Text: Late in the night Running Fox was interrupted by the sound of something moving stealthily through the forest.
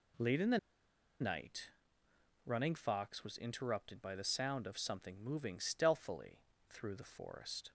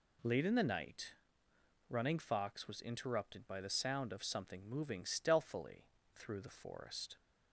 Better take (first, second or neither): second